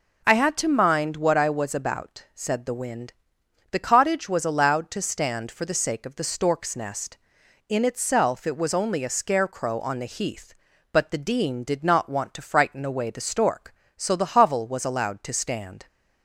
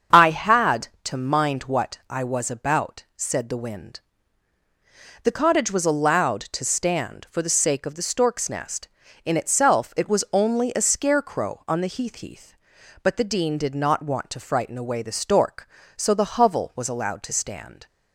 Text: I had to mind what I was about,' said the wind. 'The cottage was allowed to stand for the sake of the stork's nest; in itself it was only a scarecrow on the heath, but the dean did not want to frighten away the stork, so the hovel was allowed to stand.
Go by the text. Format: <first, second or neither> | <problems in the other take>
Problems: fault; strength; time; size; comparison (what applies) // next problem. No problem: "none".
first | starts louder than the rest; until 1.3 s; 7 dB // says "heath" twice; at 12.1 s